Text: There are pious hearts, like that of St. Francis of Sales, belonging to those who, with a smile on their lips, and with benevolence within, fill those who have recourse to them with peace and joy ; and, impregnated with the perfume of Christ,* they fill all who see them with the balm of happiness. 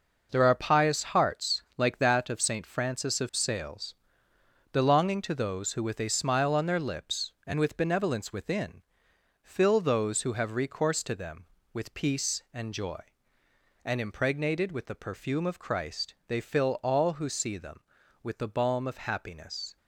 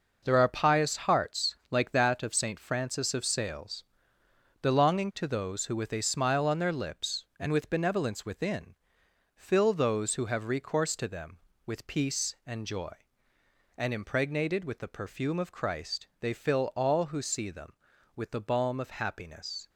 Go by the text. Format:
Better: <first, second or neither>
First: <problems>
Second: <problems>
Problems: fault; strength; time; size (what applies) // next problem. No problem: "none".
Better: neither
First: none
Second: none